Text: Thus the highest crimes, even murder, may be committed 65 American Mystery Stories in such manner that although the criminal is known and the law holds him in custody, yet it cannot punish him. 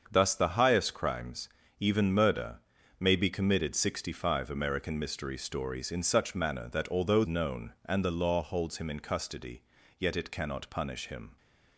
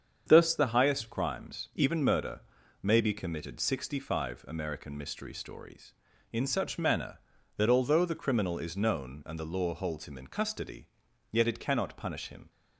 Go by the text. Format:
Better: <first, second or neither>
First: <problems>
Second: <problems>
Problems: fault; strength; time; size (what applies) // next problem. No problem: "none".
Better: second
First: starts louder than the rest; until 1.1 s; 7 dB // skips "the criminal is"; at 7.2 s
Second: starts louder than the rest; strong; until 1.2 s; 7.5 dB